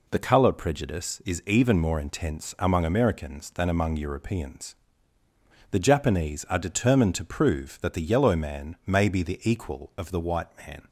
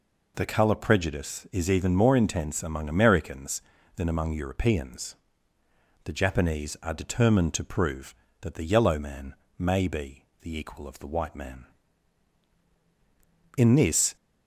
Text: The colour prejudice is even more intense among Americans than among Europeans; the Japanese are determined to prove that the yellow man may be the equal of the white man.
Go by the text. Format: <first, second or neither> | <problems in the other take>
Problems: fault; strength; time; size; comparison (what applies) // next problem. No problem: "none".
first | pauses between "man" and "may"; slight; at 9.3 s; 0.24 s long // pauses between "be" and "the"; slight; at 10.2 s; 0.16 s long // goes on to say "In this"; from 13.5 s on; 0.60 s long